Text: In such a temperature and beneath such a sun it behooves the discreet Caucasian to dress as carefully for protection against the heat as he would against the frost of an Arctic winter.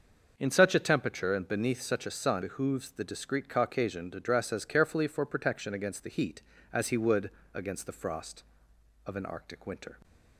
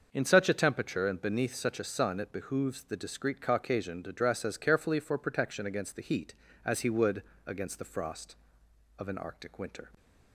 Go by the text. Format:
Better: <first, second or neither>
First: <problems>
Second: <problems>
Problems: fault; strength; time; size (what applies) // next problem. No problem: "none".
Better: second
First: starts louder than the rest; until 1.3 s; 6.5 dB // skips "it"; at 2.4 s // pauses between "would" and "against"; slight; at 7.2 s; 0.24 s long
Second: starts louder than the rest; until 1.1 s; 6.5 dB // pauses between "would" and "against"; slight; at 7.2 s; 0.24 s long